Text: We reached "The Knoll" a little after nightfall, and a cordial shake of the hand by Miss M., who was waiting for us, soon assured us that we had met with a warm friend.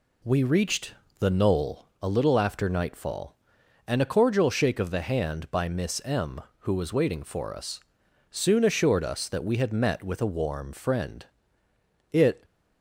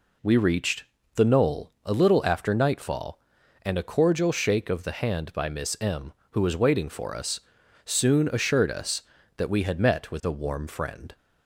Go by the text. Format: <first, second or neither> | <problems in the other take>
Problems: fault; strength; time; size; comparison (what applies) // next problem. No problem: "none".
second | pauses between "reached" and "The"; slight; at 0.9 s; 0.26 s long; slight in the second // pauses between "Knoll" and "a"; slight; at 1.8 s; 0.15 s long // goes on to say "It"; slight; from 12.1 s on; 0.32 s long